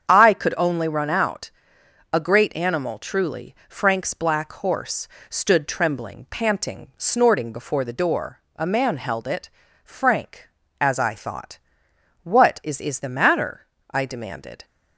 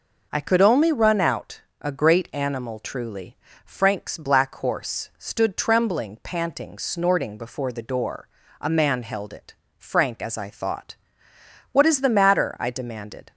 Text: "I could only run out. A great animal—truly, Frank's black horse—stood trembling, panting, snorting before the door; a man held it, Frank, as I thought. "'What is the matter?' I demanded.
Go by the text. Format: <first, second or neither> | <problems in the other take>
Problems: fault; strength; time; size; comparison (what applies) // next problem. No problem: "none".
second | starts louder than the rest; strong; until 1.1 s; 8 dB // says "is" twice; at 12.8 s